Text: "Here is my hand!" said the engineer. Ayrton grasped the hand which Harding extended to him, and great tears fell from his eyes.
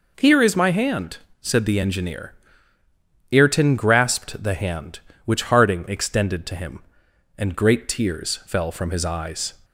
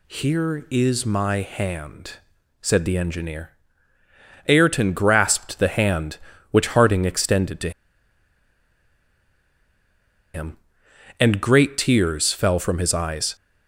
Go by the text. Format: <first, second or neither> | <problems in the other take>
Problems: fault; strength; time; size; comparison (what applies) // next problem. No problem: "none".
first | pauses between "to" and "him"; strong; at 7.6 s; 2.6 s long